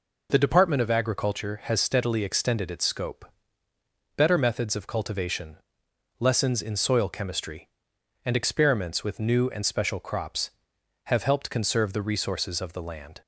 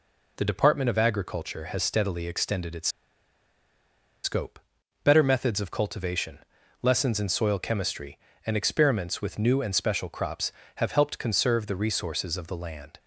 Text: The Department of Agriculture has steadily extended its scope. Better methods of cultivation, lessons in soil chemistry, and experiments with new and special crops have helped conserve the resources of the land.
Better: first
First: none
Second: pauses between "its" and "scope"; strong; at 2.8 s; 1.3 s long

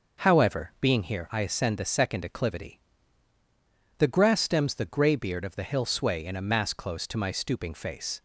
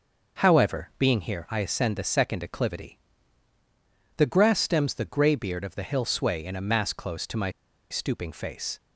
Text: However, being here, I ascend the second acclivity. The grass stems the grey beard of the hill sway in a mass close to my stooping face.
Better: first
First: none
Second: pauses between "my" and "stooping"; at 7.4 s; 0.41 s long

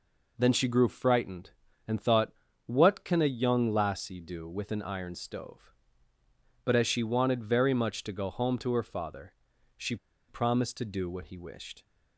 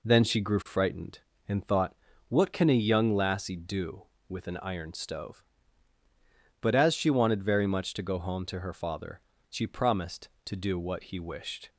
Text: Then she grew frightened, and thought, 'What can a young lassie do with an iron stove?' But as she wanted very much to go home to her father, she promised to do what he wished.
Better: second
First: pauses between "she" and "promised"; slight; at 9.9 s; 0.32 s long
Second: none

